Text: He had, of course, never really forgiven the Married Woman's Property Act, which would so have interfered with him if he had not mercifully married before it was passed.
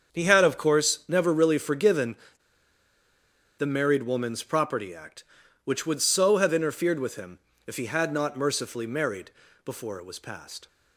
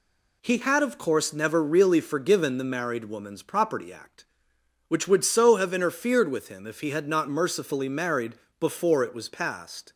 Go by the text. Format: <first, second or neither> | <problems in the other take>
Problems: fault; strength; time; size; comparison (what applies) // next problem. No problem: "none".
second | starts louder than the rest; strong; until 1.2 s; 7.5 dB // pauses between "forgiven" and "the"; strong; at 2.1 s; 1.4 s long // pauses between "him" and "if"; slight; at 7.3 s; 0.28 s long // pauses between "married" and "before"; slight; at 9.3 s; 0.34 s long; slight in the second